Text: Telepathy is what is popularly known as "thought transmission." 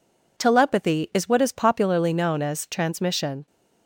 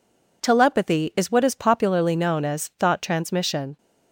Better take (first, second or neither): second